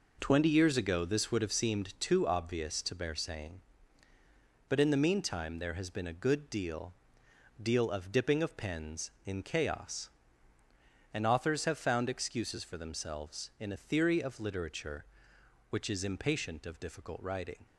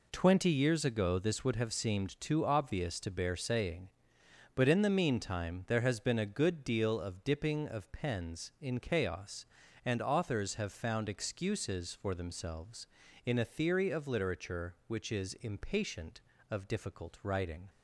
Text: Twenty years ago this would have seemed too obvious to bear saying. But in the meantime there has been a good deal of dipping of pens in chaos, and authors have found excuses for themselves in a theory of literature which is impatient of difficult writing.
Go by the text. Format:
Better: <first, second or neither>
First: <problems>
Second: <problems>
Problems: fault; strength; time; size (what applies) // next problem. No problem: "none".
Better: second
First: says "deal" twice; at 7.6 s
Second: none